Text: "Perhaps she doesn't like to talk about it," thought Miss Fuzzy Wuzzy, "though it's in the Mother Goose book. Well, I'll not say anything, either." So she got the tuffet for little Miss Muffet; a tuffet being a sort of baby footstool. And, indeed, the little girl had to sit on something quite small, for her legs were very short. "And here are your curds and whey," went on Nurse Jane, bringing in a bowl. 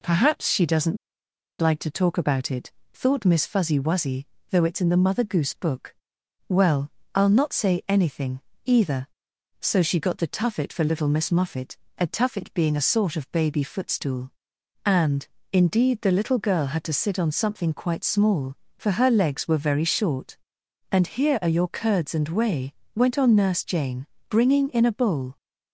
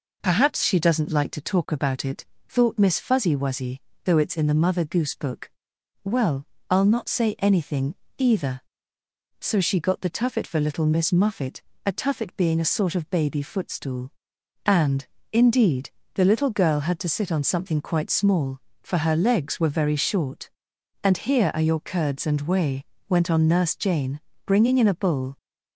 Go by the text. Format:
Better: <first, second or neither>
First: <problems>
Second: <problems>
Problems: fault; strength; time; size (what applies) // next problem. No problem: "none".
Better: second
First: pauses between "doesn't" and "like"; noticeable; at 0.9 s; 0.65 s long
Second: none